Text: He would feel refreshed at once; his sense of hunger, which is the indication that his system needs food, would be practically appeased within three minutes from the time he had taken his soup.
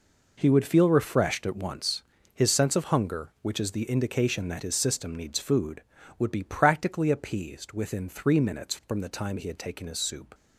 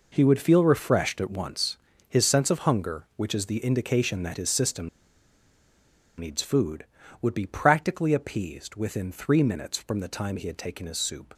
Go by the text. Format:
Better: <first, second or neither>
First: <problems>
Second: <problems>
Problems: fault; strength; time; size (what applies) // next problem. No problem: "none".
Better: first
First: none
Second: pauses between "system" and "needs"; strong; at 4.8 s; 1.3 s long